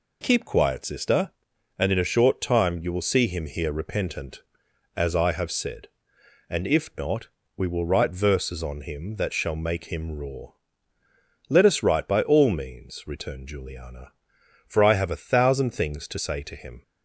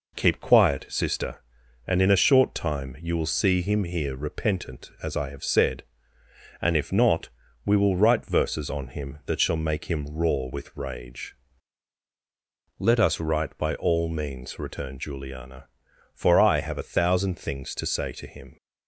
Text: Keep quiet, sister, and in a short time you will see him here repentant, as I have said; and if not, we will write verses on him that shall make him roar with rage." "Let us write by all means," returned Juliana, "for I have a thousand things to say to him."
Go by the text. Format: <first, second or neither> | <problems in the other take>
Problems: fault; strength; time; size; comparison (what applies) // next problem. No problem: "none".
second | skips "with rage"; at 11.0 s